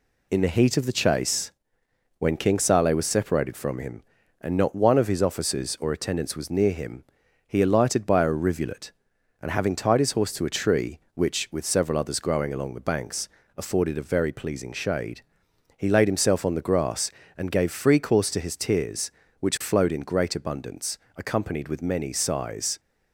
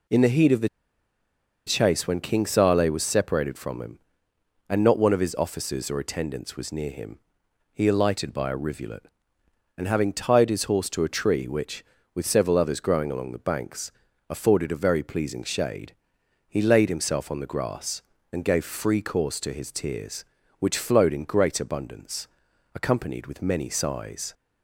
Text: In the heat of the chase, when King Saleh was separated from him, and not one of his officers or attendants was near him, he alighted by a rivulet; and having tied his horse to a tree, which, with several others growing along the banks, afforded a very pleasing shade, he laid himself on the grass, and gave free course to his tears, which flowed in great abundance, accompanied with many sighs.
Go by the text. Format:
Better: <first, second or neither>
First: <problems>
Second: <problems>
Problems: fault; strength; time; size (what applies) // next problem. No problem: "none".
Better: first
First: none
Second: pauses between "the" and "chase"; at 0.6 s; 0.98 s long